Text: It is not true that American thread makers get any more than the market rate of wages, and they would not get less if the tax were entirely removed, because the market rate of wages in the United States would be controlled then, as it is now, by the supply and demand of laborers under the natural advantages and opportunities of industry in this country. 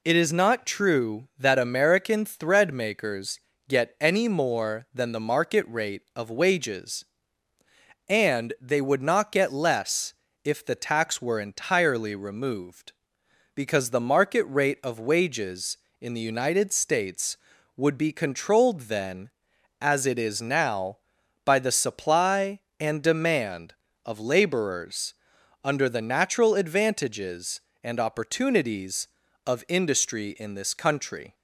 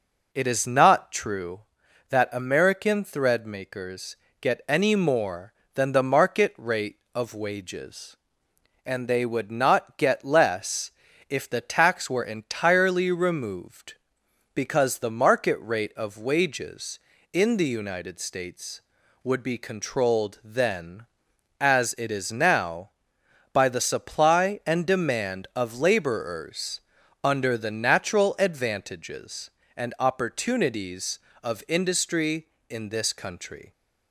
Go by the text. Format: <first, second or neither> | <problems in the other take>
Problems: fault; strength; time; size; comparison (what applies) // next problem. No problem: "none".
neither | pauses between "makers" and "get"; slight; the same in both // pauses between "less" and "if"; the same in both // pauses between "laborers" and "under"; the same in both